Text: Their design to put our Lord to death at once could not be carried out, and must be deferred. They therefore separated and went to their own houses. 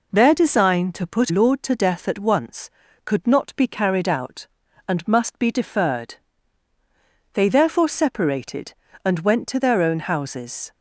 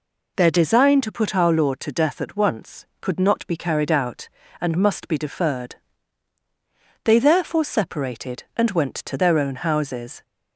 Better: second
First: skips "our"; at 1.3 s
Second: none

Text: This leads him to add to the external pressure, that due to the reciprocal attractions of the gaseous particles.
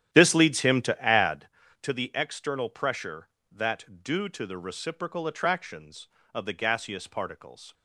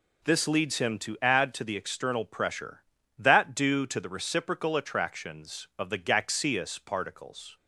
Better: second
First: starts louder than the rest; strong; until 1.6 s; 11 dB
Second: none

